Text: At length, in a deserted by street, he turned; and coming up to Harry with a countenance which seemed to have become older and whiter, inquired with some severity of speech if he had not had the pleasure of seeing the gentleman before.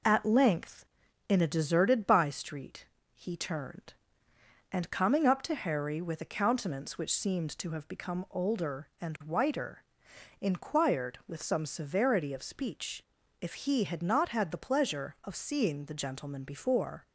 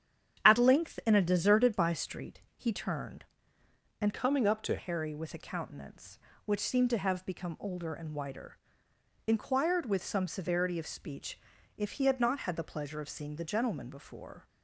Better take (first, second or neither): first